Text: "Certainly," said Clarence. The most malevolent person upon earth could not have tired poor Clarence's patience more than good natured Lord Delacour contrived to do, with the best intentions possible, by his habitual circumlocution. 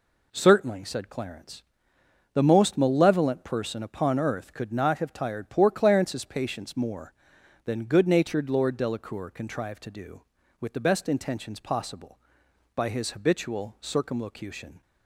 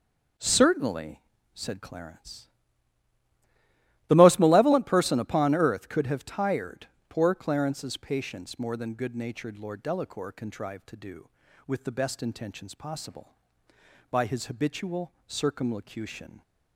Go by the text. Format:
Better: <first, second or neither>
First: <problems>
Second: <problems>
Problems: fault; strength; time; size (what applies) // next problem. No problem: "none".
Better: first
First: none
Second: skips "not"; at 6.0 s // pauses between "tired" and "poor"; slight; at 6.8 s; 0.20 s long // pauses between "habitual" and "circumlocution"; slight; at 15.1 s; 0.16 s long